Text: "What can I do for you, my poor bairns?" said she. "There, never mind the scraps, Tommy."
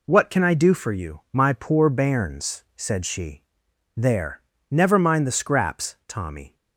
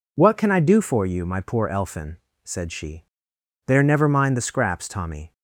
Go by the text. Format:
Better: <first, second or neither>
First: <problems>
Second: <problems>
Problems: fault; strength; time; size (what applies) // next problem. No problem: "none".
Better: first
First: none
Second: says "elfin" for "bairns"; at 1.6 s